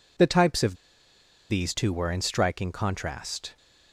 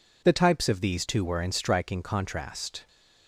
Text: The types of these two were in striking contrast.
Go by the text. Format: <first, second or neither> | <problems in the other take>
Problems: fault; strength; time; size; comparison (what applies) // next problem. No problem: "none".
second | pauses between "of" and "these"; noticeable; at 0.7 s; 0.75 s long